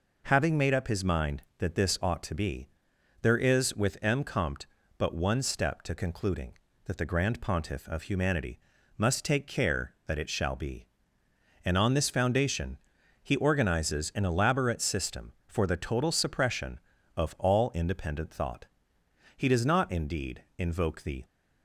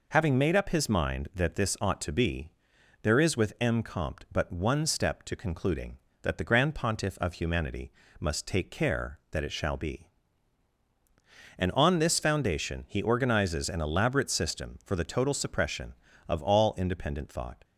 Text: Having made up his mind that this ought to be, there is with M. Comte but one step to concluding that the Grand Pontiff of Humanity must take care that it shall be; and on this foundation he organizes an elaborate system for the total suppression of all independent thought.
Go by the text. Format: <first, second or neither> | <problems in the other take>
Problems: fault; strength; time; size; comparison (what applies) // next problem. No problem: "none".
second | pauses between "Humanity" and "must"; at 8.5 s; 0.40 s long; slight in the second // pauses between "foundation" and "he"; at 12.7 s; 0.42 s long // goes on to say "He does not indeed invoke the"; strong; from 19.3 s on; 1.8 s long